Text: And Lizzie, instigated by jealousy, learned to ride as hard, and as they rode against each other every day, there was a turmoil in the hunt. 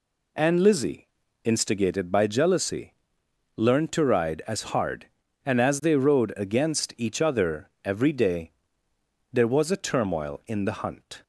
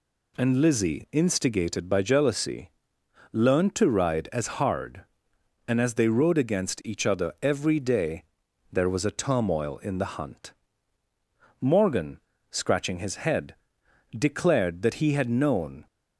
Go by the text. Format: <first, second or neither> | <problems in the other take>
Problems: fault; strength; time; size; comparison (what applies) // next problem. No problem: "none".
first | goes on to say "Morgan scratching his head declared that he had known"; strong; from 11.5 s on; 4.2 s long